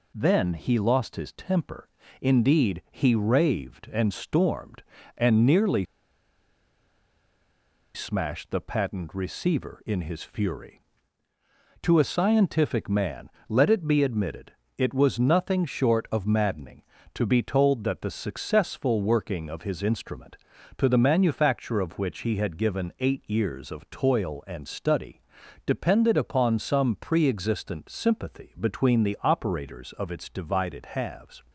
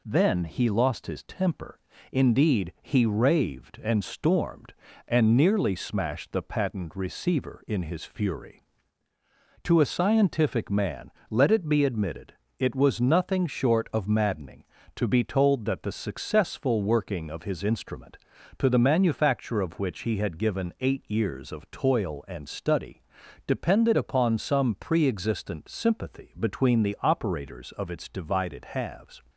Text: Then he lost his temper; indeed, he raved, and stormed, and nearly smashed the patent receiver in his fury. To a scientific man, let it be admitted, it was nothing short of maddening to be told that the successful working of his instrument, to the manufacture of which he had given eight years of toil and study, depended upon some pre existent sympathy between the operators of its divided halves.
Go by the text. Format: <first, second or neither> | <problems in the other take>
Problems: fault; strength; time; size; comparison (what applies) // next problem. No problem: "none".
second | pauses between "nearly" and "smashed"; strong; at 5.8 s; 2.0 s long